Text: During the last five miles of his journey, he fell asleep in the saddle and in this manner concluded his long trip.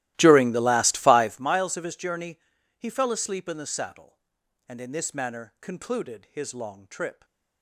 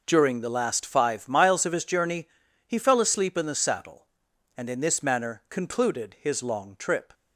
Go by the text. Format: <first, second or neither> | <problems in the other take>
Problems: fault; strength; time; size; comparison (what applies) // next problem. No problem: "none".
second | starts louder than the rest; strong; until 1.5 s; 16 dB